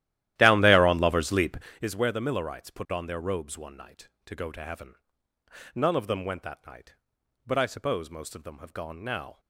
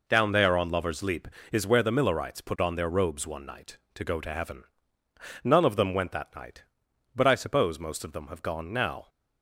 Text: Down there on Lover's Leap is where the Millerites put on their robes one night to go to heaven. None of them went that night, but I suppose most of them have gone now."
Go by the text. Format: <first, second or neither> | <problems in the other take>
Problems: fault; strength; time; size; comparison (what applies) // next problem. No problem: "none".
second | starts louder than the rest; strong; until 1.8 s; 13.5 dB